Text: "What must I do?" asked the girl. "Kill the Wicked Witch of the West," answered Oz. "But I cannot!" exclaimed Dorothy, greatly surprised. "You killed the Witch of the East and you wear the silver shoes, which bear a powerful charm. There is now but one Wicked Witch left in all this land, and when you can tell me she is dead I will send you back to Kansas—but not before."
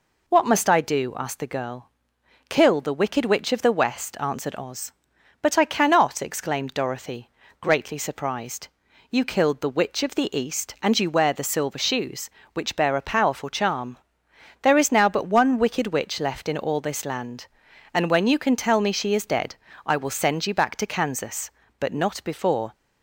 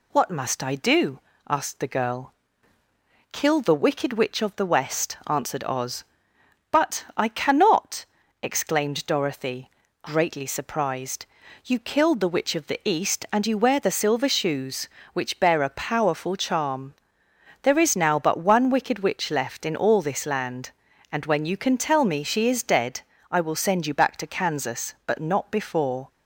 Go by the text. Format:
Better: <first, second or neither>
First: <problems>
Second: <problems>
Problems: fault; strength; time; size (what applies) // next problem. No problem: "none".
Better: neither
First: pauses between "dead" and "I"; slight; at 19.5 s; 0.30 s long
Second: pauses between "dead" and "I"; slight; at 23.0 s; 0.28 s long